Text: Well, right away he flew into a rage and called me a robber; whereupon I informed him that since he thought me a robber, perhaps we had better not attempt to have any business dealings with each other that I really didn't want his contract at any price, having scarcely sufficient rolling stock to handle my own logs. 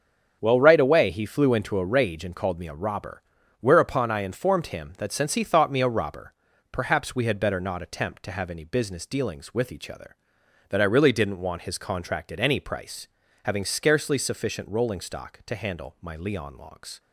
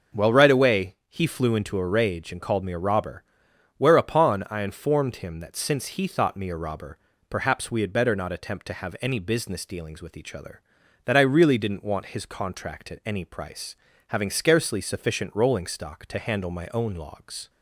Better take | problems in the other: second | starts louder than the rest; strong; until 1.4 s; 7.5 dB // says "leon" for "own"; at 16.1 s

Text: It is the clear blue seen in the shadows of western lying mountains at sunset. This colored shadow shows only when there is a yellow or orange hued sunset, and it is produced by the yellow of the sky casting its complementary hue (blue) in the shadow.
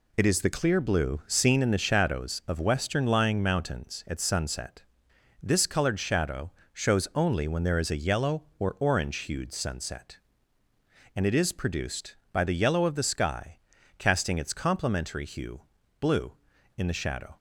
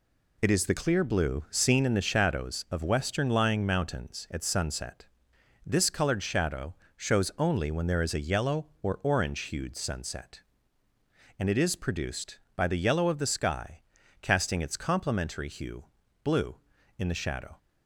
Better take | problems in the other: neither | pauses between "shadow" and "shows"; slight; the same in both // pauses between "sky" and "casting"; the same in both

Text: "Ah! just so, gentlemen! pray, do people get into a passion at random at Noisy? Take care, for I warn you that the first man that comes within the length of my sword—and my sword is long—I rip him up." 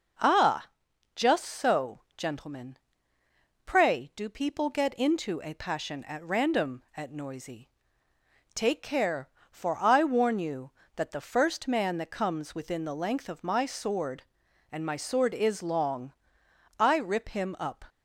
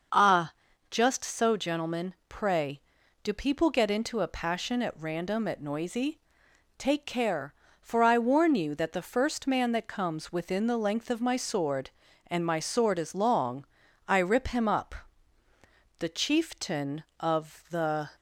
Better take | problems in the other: first | starts louder than the rest; until 1.5 s; 6.5 dB // goes on to say "The chieftain of the"; strong; from 15.9 s on; 2.1 s long

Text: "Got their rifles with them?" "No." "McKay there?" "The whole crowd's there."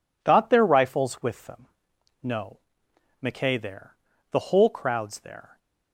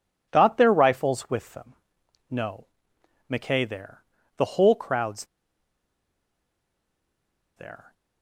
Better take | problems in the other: first | pauses between "crowd's" and "there"; strong; at 5.2 s; 2.3 s long

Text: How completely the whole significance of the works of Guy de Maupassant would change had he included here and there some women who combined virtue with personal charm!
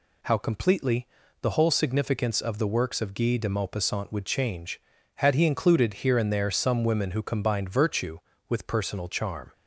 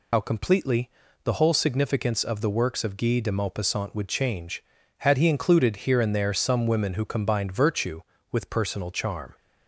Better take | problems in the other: first | loses the start of "How"; at 0.1 s; 70 ms // pauses between "completely" and "the"; slight; at 0.8 s; 0.34 s long; slight in the first

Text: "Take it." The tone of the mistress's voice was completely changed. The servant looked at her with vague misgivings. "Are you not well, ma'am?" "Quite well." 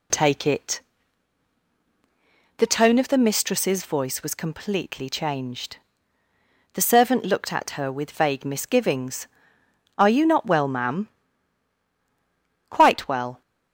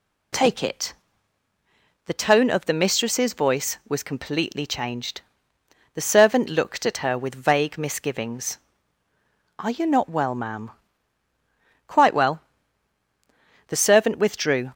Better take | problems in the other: first | goes on to say "The servant withdrew"; noticeable; from 13.6 s on; 1.0 s long

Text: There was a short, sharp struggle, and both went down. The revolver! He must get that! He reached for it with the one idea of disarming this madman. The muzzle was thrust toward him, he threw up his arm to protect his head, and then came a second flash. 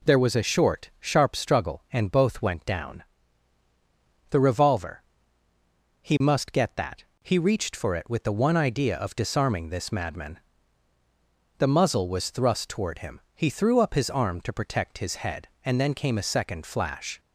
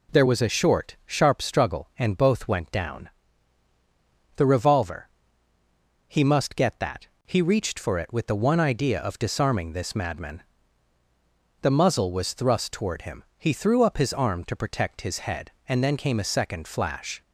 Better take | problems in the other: neither | none

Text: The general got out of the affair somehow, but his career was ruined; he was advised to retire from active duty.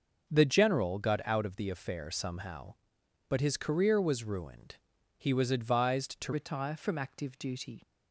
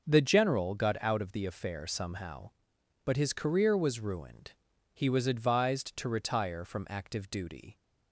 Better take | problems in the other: second | starts louder than the rest; until 1.3 s; 6 dB; noticeable in the second // changes voice at "retire"; from 6.3 s on; 1.5 s long

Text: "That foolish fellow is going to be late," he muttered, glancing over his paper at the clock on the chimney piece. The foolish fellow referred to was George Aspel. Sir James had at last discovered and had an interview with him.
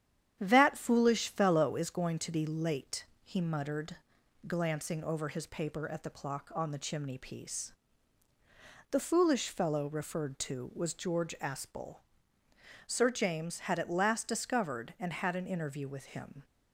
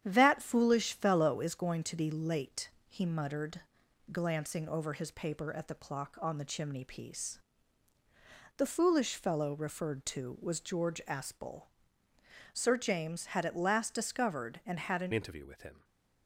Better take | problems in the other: first | starts louder than the rest; strong; until 1.0 s; 9.5 dB; strong in the first // changes voice at "interview"; from 15.1 s on; 0.7 s long

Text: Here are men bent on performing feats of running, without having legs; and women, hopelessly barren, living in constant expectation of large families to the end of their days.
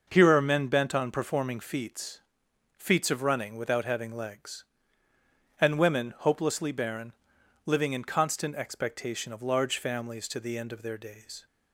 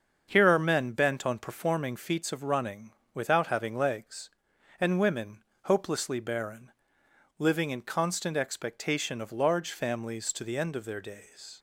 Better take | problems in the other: second | starts louder than the rest; noticeable; until 1.1 s; 6 dB; also in the second // says "feats" twice; at 2.7 s

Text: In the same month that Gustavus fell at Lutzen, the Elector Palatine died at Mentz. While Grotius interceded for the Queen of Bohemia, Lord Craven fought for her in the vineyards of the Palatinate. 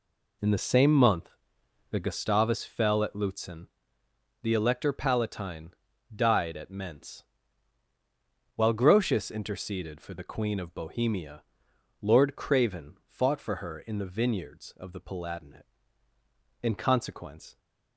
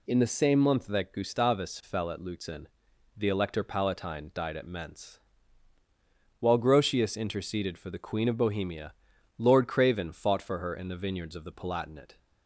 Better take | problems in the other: second | pauses between "Palatine" and "died"; at 5.7 s; 0.44 s long // goes on to say "In consequence"; noticeable; from 16.6 s on; 0.96 s long

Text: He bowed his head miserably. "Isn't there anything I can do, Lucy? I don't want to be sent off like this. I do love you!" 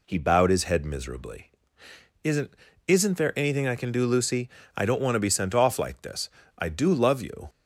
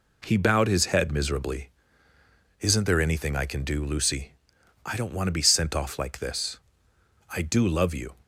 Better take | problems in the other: second | says "Isn't" twice; at 2.8 s

